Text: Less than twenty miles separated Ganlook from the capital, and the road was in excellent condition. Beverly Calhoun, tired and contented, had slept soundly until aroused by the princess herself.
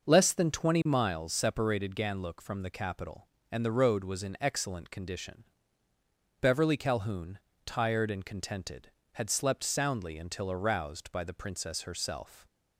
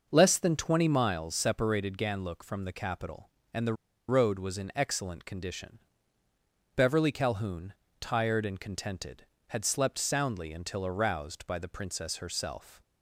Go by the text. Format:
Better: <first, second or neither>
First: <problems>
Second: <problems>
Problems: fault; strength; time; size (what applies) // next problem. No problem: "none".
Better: first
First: starts louder than the rest; noticeable; until 1.0 s; 6 dB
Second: starts louder than the rest; noticeable; until 1.1 s; 6 dB // pauses between "the" and "road"; slight; at 3.7 s; 0.34 s long